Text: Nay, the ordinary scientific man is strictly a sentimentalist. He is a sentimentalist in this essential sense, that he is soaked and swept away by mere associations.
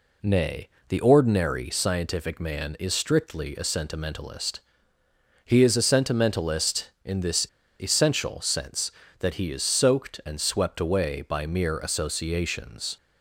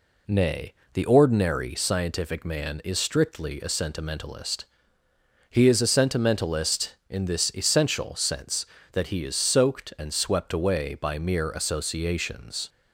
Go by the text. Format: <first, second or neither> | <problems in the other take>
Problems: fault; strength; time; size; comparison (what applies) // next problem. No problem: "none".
second | pauses between "this" and "essential"; slight; at 7.4 s; 0.34 s long